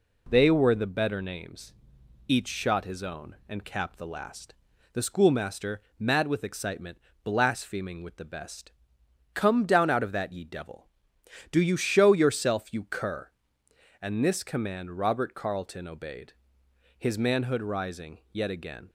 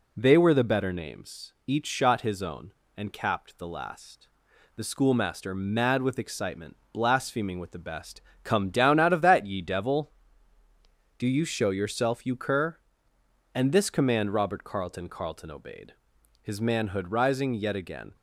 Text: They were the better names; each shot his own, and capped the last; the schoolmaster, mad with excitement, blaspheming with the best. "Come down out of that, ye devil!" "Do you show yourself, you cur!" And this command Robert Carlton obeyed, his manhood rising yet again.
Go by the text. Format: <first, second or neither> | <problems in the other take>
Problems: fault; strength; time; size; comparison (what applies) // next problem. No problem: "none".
first | says "Carlton" twice; at 15.0 s